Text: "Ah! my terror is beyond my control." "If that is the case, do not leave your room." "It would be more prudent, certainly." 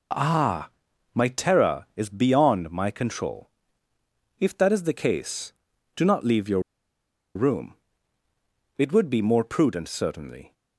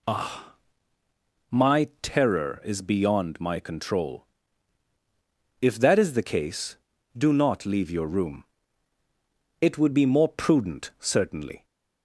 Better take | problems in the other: second | pauses between "your" and "room"; noticeable; at 6.5 s; 0.75 s long

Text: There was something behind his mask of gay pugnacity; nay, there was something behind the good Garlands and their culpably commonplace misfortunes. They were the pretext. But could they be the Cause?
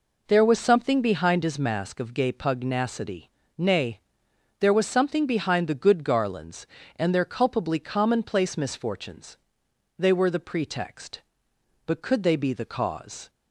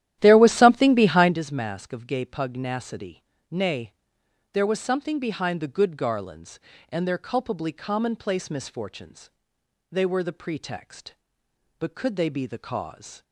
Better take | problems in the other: first | starts louder than the rest; strong; until 1.4 s; 12.5 dB

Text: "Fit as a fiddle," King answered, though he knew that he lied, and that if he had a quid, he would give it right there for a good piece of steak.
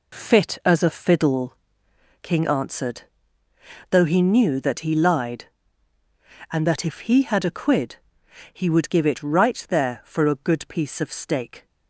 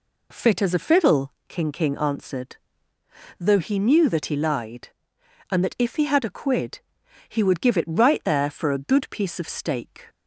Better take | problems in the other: first | says "King" twice; at 1.7 s

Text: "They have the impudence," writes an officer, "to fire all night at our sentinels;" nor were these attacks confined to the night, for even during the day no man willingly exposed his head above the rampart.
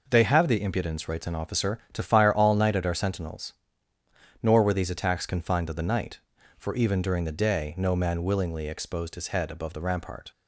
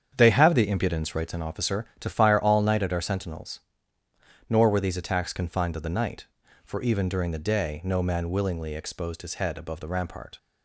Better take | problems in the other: first | starts louder than the rest; strong; until 1.3 s; 8 dB

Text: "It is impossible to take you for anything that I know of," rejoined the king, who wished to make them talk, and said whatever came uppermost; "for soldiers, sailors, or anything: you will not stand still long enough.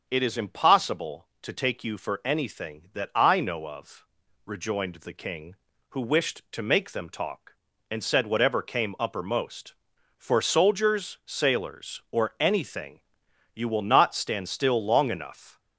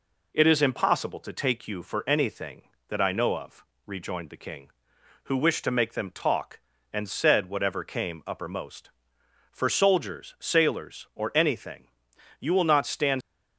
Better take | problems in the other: first | stops before "still long enough"; at 13.2 s

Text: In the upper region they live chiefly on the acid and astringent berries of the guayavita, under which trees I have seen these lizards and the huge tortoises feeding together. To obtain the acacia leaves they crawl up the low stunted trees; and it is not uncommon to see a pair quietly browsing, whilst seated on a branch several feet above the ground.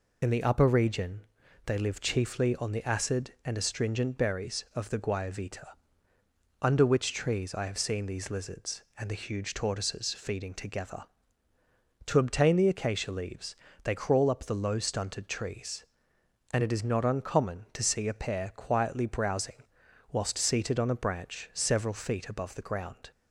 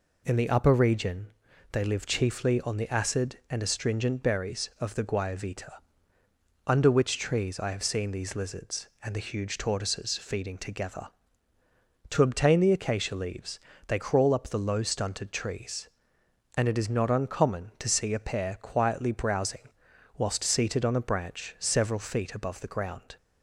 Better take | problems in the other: second | loses the start of "In"; at 0.2 s; 30 ms // pauses between "region" and "they"; noticeable; at 1.2 s; 0.46 s long; noticeable in the second // pauses between "leaves" and "they"; slight; at 13.5 s; 0.30 s long; slight in the second

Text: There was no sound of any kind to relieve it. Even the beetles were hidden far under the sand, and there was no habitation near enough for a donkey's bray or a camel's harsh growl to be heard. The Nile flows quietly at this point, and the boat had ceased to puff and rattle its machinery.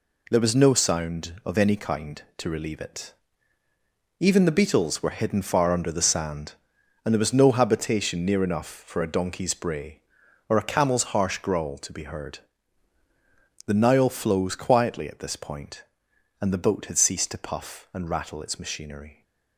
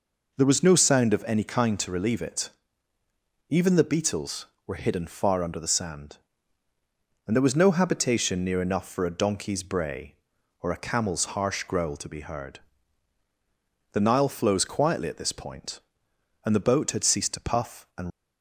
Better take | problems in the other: first | stops before "rattle its machinery"; at 18.1 s

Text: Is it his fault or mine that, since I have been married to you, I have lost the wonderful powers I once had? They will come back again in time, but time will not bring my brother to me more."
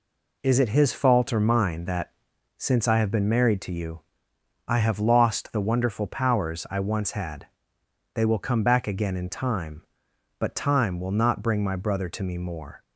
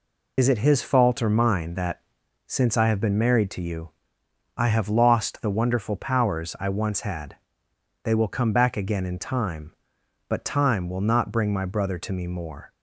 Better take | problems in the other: first | loses the start of "Is"; at 0.3 s; 65 ms

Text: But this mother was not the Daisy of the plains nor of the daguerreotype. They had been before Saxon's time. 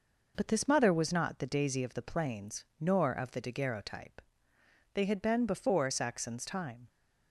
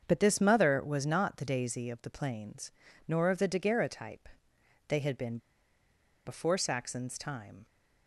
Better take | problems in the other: first | starts louder than the rest; until 1.0 s; 7 dB // pauses between "plains" and "nor"; slight; at 2.7 s; 0.36 s long // pauses between "been" and "before"; noticeable; at 5.3 s; 0.88 s long

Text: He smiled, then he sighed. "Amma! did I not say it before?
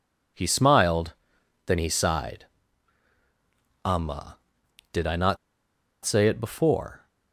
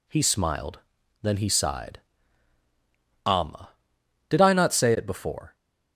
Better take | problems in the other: second | pauses between "not" and "say"; noticeable; at 5.3 s; 0.68 s long

